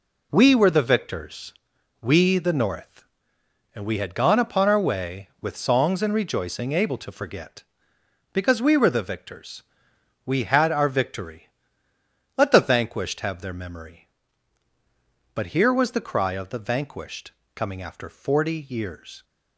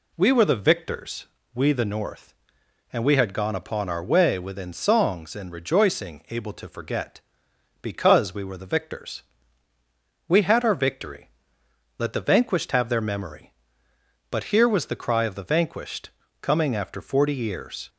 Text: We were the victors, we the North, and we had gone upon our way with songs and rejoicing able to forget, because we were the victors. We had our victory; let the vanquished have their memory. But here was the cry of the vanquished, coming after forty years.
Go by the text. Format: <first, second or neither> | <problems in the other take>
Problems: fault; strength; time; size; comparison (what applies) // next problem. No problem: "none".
first | says "within" for "with"; at 4.3 s